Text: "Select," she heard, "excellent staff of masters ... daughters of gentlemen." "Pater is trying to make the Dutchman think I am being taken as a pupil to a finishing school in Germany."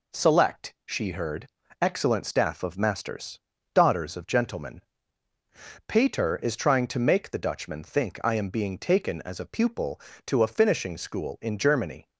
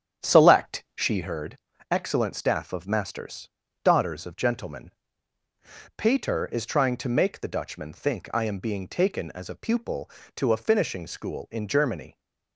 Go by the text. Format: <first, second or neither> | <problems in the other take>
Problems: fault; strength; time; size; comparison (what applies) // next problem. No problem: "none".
first | starts louder than the rest; strong; until 1.3 s; 9 dB